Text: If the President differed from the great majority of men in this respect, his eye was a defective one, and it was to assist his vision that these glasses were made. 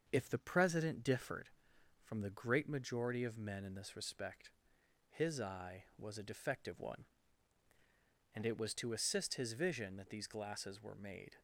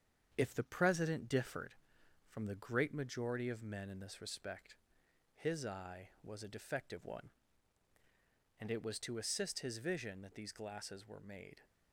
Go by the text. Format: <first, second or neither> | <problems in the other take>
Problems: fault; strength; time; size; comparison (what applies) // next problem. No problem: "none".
first | gets quieter; slight; throughout; 3 dB // starts louder than the rest; strong; until 1.3 s; 7.5 dB; also in the first